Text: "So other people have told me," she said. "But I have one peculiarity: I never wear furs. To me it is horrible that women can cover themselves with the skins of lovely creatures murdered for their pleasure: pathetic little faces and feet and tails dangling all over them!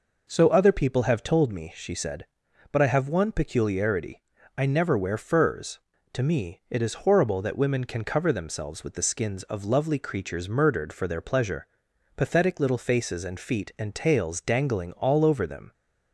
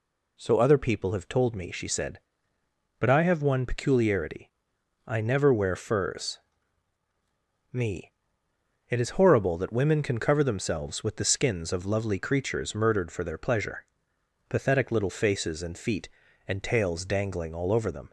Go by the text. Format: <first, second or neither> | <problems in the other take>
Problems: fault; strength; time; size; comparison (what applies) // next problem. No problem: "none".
first | skips "To"; at 7.0 s // pauses between "me" and "it"; noticeable; at 8.1 s; 0.78 s long